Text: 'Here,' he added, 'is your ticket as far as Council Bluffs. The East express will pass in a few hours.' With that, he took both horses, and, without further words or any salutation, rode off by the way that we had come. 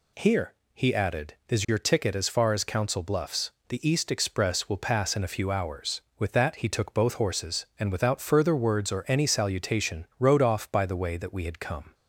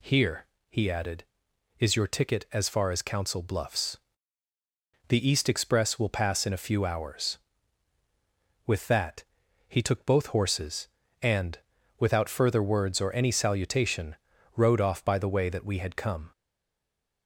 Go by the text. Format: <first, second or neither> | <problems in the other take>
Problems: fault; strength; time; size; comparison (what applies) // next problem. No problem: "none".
first | stays silent after the last word; slight; from 16.3 s on; 0.9 s long